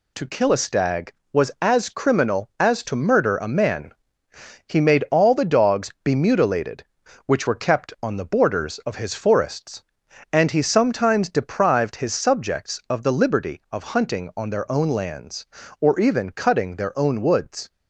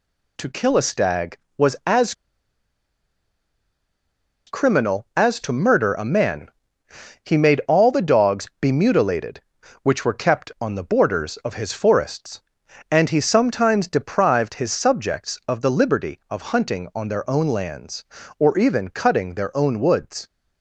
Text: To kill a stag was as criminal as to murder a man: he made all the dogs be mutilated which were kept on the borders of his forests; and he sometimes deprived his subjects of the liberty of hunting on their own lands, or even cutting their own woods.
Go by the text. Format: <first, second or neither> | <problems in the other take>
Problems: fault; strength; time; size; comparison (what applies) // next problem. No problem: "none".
first | pauses between "as" and "criminal"; strong; at 2.1 s; 2.3 s long